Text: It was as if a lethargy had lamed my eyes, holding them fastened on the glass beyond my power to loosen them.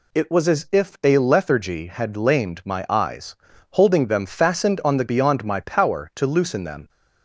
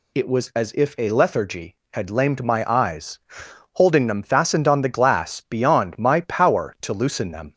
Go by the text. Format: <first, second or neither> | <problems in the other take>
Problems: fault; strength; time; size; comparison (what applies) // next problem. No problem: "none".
second | skips "glass"; at 5.0 s